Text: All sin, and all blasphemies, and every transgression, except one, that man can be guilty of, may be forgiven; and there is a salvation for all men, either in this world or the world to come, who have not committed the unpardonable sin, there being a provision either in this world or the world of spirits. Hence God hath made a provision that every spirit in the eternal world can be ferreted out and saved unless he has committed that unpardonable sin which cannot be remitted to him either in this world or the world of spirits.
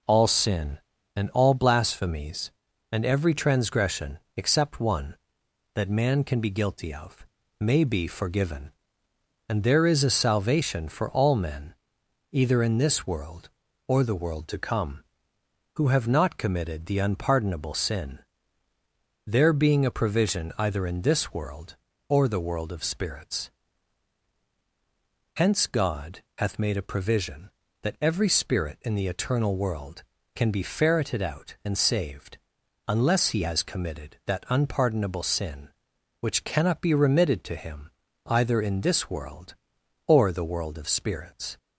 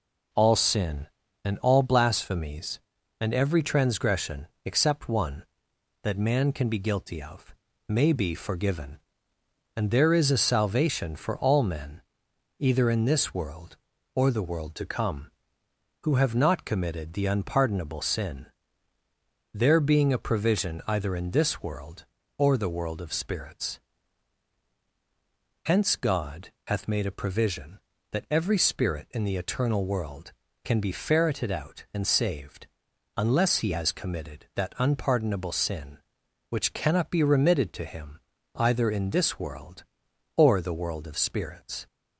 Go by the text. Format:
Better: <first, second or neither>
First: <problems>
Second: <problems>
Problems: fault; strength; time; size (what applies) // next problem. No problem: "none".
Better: neither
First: pauses between "God" and "hath"; slight; at 26.2 s; 0.16 s long // pauses between "saved" and "unless"; noticeable; at 32.3 s; 0.50 s long // pauses between "him" and "either"; at 37.8 s; 0.38 s long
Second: pauses between "God" and "hath"; slight; at 26.5 s; 0.16 s long // pauses between "saved" and "unless"; noticeable; at 32.6 s; 0.50 s long // pauses between "him" and "either"; at 38.1 s; 0.38 s long